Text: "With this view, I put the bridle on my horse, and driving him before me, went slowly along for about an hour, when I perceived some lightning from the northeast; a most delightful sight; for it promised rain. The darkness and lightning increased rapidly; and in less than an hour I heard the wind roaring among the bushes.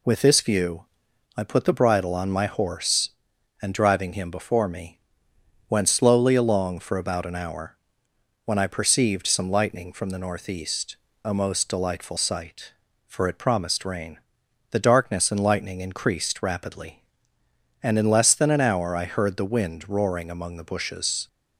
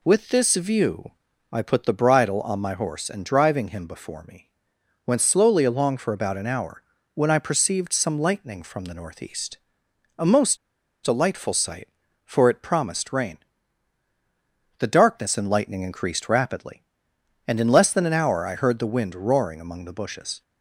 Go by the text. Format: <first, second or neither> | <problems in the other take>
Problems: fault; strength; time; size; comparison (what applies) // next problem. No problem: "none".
first | pauses between "most" and "delightful"; noticeable; at 10.5 s; 0.46 s long